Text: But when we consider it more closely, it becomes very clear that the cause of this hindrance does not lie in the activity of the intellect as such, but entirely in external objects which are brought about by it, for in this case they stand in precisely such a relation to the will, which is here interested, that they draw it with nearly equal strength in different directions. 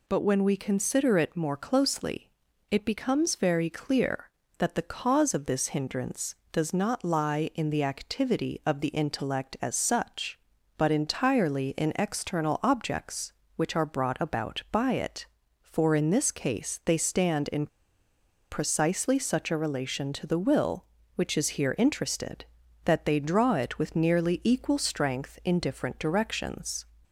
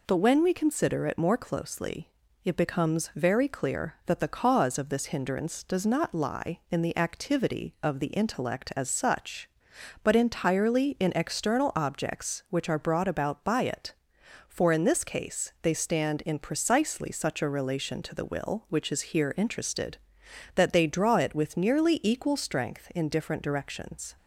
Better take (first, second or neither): second